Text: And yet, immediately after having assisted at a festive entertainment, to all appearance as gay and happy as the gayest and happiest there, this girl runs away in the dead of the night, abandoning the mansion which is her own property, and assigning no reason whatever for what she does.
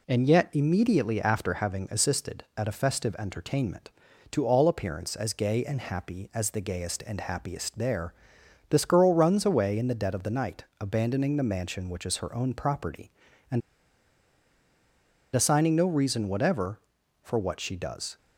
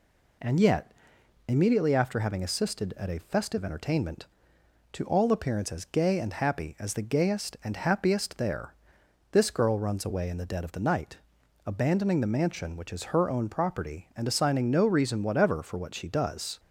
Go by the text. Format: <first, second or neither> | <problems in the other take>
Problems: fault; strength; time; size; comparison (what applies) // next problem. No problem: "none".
second | pauses between "and" and "assigning"; strong; at 13.6 s; 1.7 s long